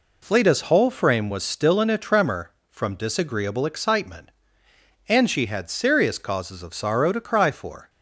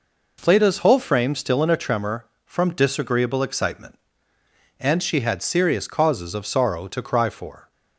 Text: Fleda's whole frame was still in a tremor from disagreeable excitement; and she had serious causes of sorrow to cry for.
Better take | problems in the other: first | skips "was"; at 1.3 s

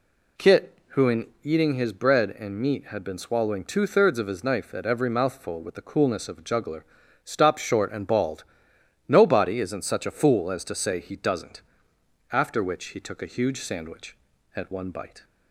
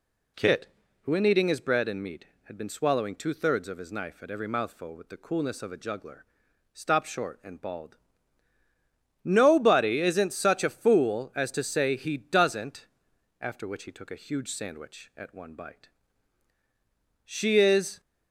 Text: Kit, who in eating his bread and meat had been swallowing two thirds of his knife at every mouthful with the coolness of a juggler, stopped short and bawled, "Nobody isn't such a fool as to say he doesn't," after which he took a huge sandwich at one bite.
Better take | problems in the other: first | goes on to say "She is"; noticeable; from 17.2 s on; 0.76 s long

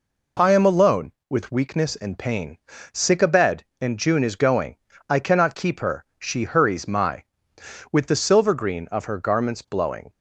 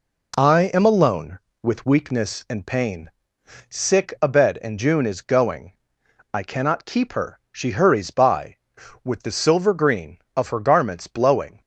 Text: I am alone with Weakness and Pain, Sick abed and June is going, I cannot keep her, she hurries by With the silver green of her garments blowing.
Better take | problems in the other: second | says "my" for "by"; at 6.8 s

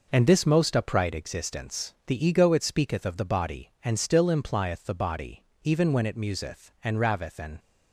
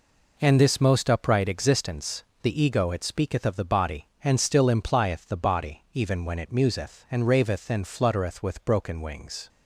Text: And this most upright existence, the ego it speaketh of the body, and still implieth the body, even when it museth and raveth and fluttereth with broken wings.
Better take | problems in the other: second | stops before "fluttereth with broken wings"; at 7.5 s

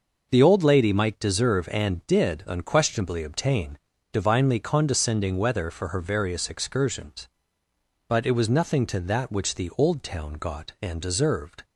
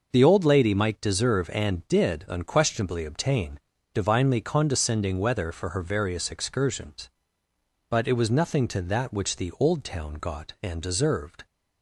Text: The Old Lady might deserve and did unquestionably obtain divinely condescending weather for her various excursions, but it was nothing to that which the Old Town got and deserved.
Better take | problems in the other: neither | pauses between "obtain" and "divinely"; slight; the same in both

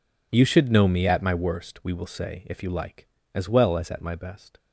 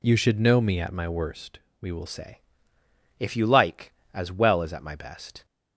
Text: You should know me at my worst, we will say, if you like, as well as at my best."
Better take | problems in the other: first | changes voice at "say"; from 2.0 s on; 3.4 s long

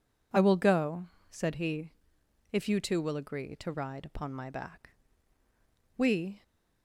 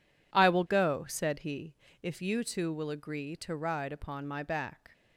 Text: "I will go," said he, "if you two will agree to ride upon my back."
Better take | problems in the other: second | goes on to say "We"; slight; from 5.9 s on; 0.46 s long

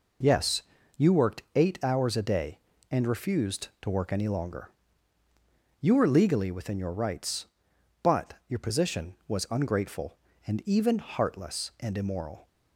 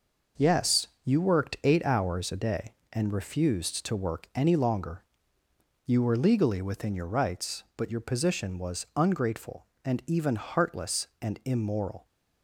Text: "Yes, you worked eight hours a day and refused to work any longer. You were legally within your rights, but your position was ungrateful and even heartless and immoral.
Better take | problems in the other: neither | none

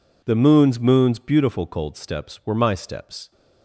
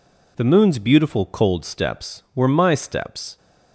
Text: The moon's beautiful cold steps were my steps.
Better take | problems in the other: second | says "moon's" twice; at 0.7 s

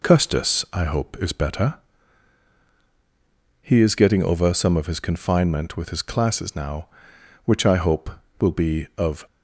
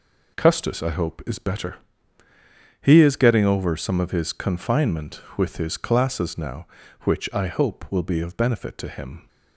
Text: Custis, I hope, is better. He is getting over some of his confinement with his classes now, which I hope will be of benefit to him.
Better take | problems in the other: second | stops before "benefit to him"; at 9.2 s

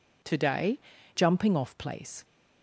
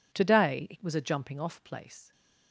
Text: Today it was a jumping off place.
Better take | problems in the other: second | skips "it was a"; at 0.9 s

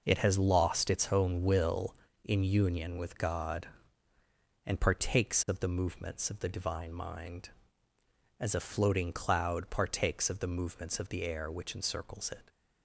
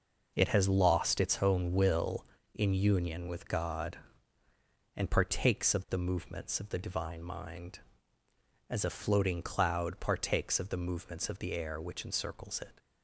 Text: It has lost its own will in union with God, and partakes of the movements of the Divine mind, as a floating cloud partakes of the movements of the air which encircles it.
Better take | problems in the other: neither | none

